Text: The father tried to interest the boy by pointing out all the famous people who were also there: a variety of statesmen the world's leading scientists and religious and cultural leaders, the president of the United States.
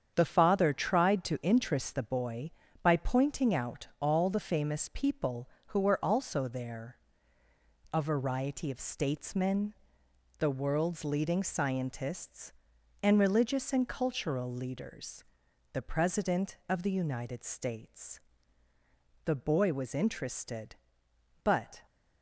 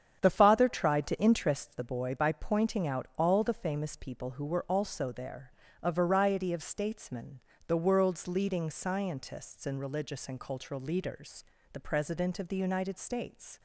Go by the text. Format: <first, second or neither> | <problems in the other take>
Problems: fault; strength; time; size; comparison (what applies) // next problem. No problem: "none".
second | starts louder than the rest; strong; until 1.1 s; 8 dB; strong in the second // pauses between "statesmen" and "the"; noticeable; at 9.7 s; 0.68 s long; slight in the second // goes on to say "The boy was interested but"; strong; from 19.2 s on; 2.5 s long